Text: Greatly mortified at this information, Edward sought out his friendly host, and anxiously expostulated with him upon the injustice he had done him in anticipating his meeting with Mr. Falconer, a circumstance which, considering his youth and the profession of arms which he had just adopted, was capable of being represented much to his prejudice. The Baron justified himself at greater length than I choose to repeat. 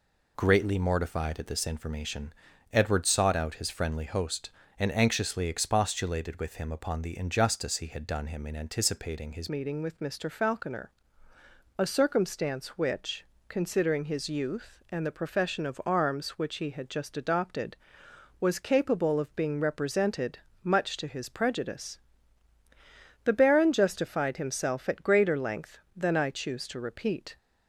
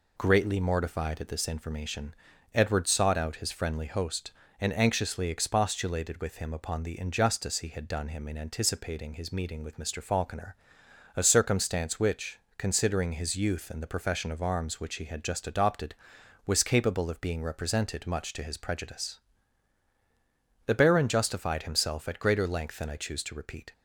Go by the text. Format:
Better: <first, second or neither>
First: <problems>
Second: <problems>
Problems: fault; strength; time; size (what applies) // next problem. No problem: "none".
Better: second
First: changes voice at "meeting"; from 9.4 s on; 17.9 s long // pauses between "represented" and "much"; slight; at 20.3 s; 0.26 s long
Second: none